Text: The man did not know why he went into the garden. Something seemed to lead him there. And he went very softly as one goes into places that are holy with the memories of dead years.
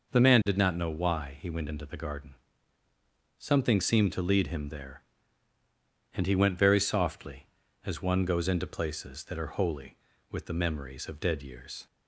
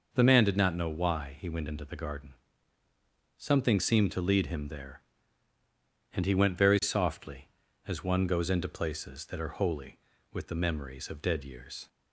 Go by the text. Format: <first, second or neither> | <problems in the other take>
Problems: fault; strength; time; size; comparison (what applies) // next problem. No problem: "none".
neither | none